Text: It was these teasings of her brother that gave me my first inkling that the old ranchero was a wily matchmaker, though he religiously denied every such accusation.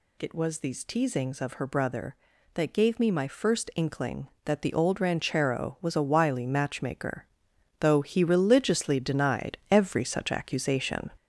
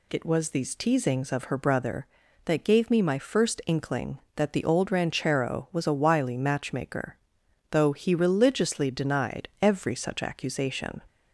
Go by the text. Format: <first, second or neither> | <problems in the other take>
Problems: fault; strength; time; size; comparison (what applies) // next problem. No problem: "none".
second | gets louder; throughout; 6.5 dB